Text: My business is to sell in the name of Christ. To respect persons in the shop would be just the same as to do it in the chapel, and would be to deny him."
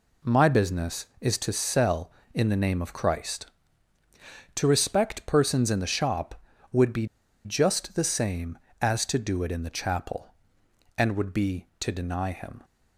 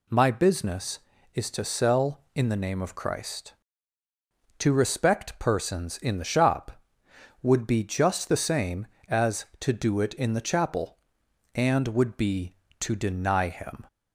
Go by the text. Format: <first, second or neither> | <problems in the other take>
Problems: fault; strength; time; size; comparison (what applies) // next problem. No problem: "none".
second | pauses between "be" and "just"; at 7.0 s; 0.39 s long